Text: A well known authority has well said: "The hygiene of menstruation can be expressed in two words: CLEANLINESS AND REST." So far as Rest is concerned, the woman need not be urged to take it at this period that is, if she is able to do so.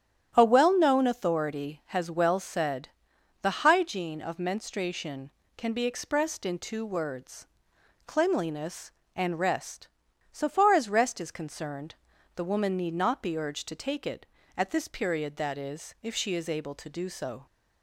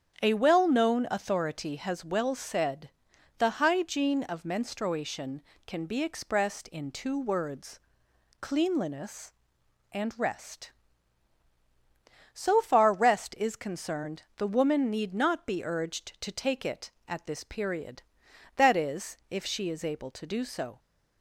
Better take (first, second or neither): first